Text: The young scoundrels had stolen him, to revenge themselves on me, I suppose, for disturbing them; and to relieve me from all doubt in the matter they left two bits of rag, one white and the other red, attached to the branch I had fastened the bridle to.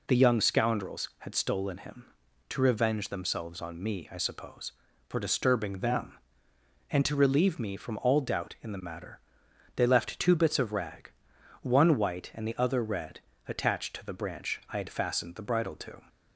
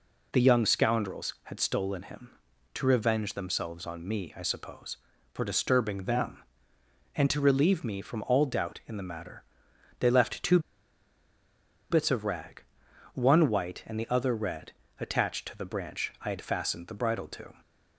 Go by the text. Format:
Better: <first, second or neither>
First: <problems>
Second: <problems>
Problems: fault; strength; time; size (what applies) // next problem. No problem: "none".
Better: first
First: pauses between "matter" and "they"; noticeable; at 9.1 s; 0.56 s long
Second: pauses between "matter" and "they"; noticeable; at 9.4 s; 0.56 s long // pauses between "two" and "bits"; strong; at 10.5 s; 1.3 s long